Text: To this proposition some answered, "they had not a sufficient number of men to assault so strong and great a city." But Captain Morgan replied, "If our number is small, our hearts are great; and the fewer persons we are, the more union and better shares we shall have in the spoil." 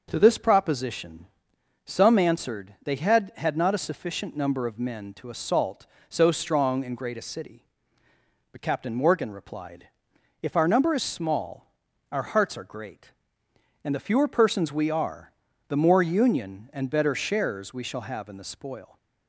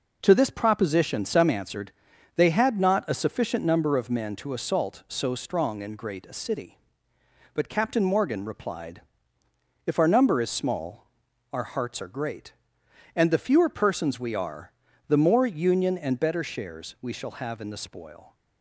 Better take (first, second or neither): second